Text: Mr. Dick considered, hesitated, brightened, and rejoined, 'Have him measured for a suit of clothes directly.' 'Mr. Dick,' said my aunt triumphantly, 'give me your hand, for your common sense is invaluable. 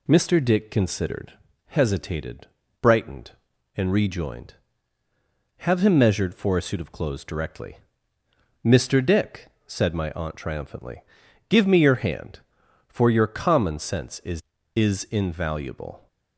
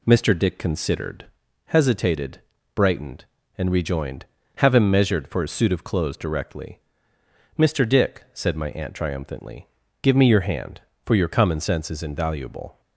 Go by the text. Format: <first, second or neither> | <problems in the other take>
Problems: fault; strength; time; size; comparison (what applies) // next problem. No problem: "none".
second | says "is" twice; at 14.7 s